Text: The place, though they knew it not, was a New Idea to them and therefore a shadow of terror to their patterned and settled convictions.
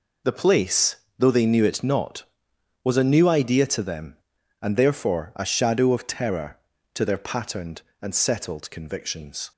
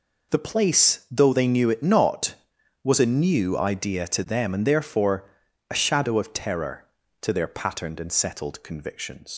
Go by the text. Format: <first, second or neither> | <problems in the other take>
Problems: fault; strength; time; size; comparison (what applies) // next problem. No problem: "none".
first | pauses between "therefore" and "a"; at 5.2 s; 0.42 s long // leaves "convictions" unfinished; at 9.3 s; 120 ms